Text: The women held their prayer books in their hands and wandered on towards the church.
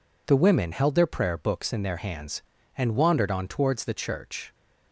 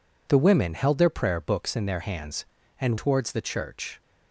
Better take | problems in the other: first | skips "wandered on"; at 2.9 s

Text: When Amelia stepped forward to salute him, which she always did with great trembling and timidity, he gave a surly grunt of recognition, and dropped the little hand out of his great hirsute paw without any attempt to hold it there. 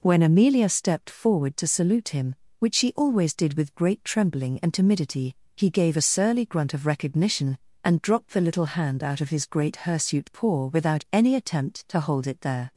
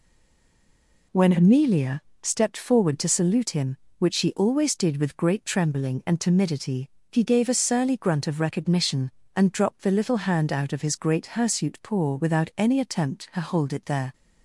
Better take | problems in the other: first | stays silent before the first word; until 1.1 s; 1.1 s long // pauses between "Amelia" and "stepped"; slight; at 2.0 s; 0.18 s long

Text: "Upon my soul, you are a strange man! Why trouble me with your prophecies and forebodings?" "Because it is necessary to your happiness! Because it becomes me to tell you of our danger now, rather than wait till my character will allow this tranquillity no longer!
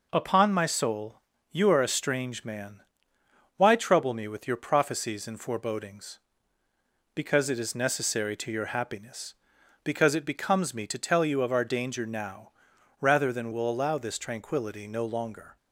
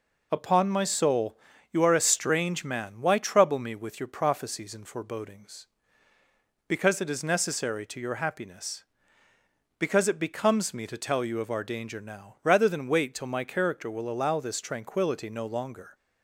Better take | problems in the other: second | skips "wait till my character"; at 13.5 s

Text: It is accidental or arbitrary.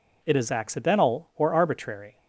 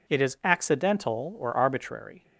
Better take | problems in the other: neither | none

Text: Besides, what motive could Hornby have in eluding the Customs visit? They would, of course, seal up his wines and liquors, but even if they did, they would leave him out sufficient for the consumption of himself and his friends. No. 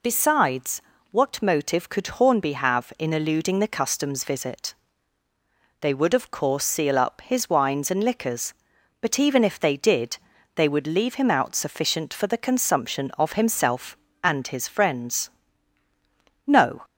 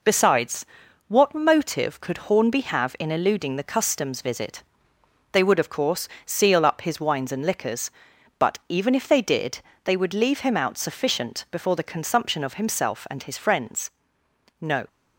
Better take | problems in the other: first | says "before" for "for"; at 11.5 s

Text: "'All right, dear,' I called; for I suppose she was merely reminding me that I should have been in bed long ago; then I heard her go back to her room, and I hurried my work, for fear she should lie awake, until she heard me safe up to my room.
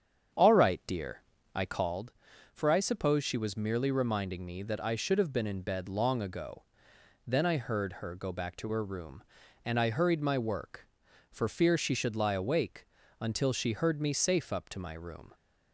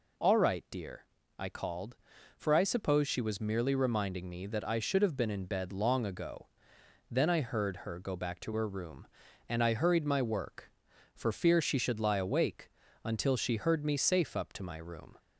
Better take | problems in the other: second | starts louder than the rest; strong; until 2.1 s; 8 dB

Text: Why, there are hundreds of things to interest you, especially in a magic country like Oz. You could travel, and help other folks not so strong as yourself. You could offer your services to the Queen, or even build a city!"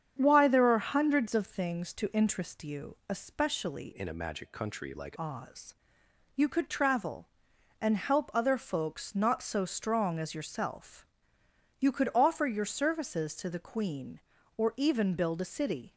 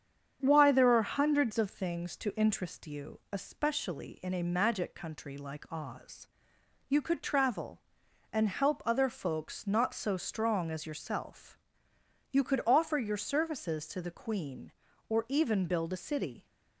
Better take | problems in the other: second | starts louder than the rest; strong; until 1.1 s; 8 dB; strong in the second // changes voice from "in" to "like"; from 3.9 to 5.1 s; 1.2 s long

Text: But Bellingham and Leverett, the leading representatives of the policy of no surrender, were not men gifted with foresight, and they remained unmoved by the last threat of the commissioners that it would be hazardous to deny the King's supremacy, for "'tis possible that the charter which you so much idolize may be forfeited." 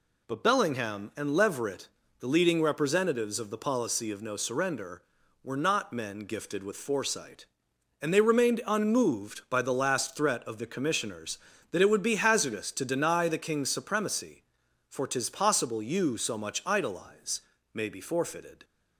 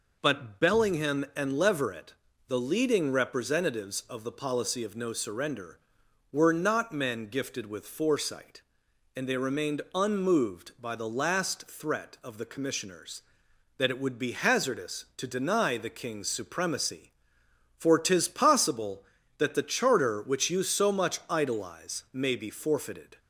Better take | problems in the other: second | skips "that the charter which"; at 15.8 s // pauses between "idolize" and "may"; slight; at 17.4 s; 0.32 s long

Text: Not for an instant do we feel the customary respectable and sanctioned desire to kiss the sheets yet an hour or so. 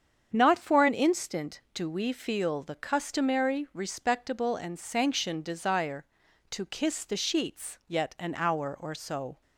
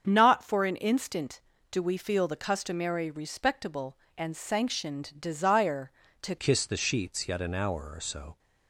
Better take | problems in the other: first | starts louder than the rest; strong; until 1.0 s; 7 dB; strong in the first // changes voice at "kiss"; from 6.3 s on; 2.0 s long

